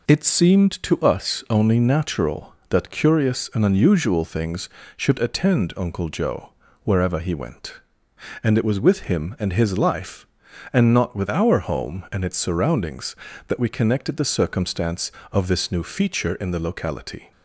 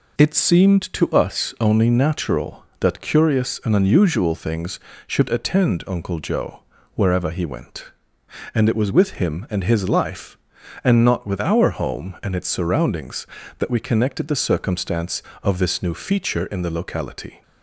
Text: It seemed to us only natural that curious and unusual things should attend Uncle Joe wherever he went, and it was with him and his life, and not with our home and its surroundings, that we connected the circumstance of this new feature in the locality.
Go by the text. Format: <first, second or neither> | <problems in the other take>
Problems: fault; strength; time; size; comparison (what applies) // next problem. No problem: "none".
neither | pauses between "Joe" and "wherever"; slight; the same in both